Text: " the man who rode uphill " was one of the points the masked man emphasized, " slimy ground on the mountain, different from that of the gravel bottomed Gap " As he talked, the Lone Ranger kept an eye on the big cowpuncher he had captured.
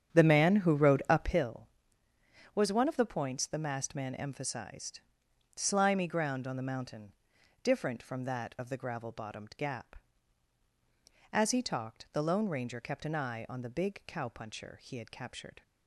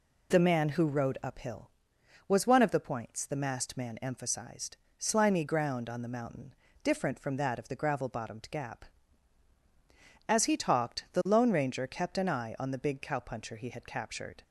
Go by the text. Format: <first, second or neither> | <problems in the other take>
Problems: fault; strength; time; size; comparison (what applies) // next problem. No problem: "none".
second | starts louder than the rest; strong; until 1.5 s; 9.5 dB